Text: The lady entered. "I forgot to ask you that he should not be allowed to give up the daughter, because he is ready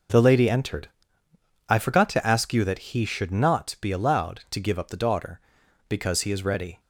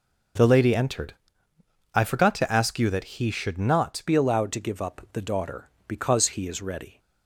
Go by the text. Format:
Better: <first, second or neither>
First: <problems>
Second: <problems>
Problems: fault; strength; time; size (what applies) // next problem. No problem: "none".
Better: first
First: none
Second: changes voice at "be"; from 4.0 s on; 2.9 s long